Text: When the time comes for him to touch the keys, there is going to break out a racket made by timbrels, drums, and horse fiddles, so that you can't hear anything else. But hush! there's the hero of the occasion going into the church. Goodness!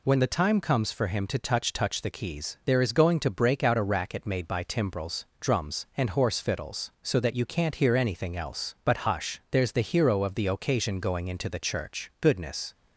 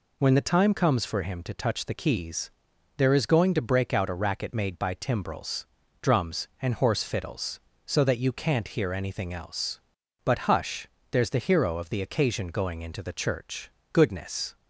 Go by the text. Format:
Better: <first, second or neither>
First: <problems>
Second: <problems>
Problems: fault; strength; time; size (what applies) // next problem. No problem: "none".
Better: second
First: says "touch" twice; at 1.7 s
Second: none